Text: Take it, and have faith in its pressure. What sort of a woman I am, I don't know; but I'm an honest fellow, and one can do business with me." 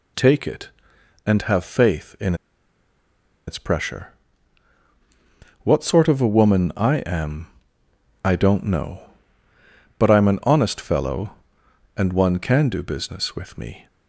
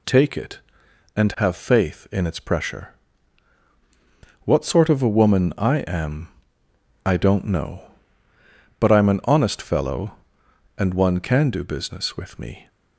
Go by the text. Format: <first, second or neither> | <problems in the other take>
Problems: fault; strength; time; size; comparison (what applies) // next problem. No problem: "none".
second | pauses between "in" and "its"; at 2.3 s; 1.1 s long